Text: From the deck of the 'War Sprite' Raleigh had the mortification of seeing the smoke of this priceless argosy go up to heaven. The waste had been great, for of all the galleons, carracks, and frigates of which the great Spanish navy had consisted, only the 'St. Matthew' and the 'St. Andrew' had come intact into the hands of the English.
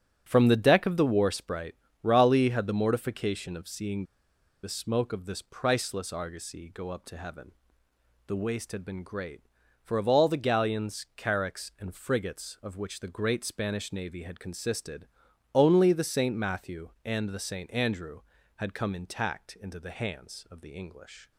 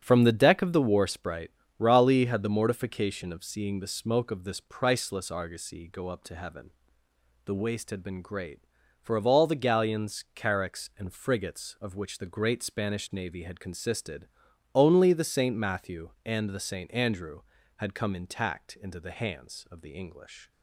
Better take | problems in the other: second | starts louder than the rest; strong; until 1.2 s; 8 dB; strong in the second // pauses between "Sprite" and "Raleigh"; slight; at 1.7 s; 0.26 s long; slight in the second // pauses between "seeing" and "the"; noticeable; at 4.0 s; 0.60 s long

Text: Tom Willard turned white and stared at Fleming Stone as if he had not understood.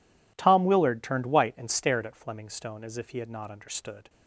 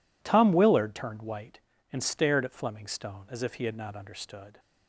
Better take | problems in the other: neither | none

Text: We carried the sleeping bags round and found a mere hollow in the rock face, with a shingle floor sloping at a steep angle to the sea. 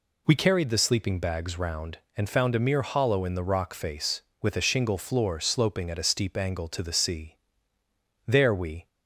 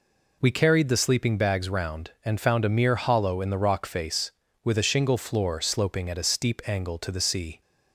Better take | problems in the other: second | goes on to say "There we"; from 8.2 s on; 0.60 s long

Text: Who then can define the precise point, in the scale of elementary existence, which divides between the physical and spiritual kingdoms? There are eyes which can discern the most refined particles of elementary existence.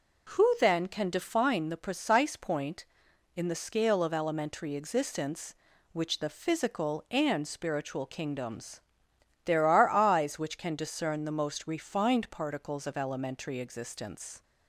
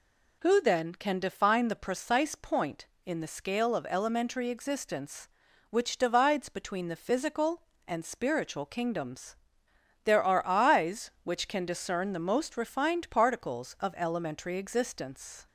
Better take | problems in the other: second | skips "divides between"; at 6.1 s

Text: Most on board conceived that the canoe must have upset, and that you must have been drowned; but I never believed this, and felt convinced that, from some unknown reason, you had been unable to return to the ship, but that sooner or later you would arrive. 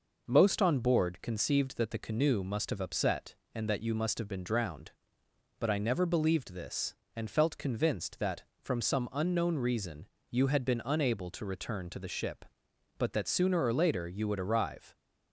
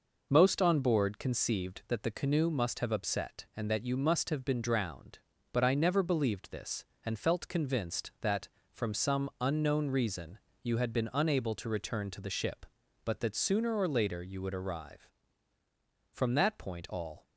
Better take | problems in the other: first | goes on to say "From that point all"; noticeable; from 16.1 s on; 1.1 s long

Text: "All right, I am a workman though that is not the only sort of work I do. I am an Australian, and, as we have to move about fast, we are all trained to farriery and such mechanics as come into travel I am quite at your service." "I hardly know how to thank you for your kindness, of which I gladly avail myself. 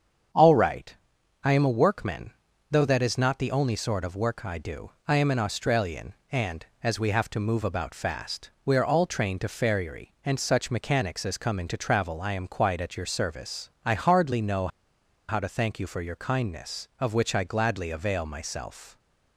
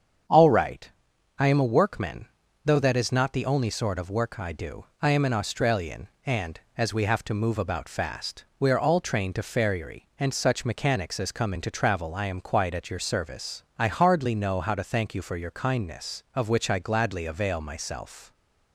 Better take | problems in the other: second | starts louder than the rest; strong; until 1.8 s; 7 dB; strong in the second // pauses between "workman" and "though"; at 2.3 s; 0.38 s long; also in the second // pauses between "know" and "how"; noticeable; at 14.6 s; 0.60 s long

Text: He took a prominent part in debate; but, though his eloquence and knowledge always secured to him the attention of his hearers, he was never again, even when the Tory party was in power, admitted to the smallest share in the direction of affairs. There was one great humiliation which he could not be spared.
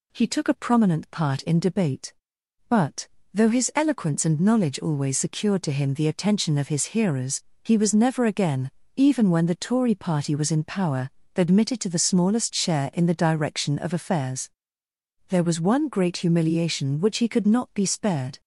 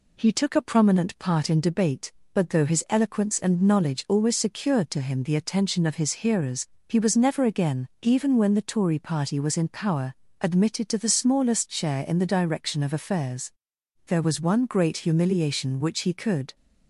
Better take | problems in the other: first | stops before "not be spared"; at 16.5 s

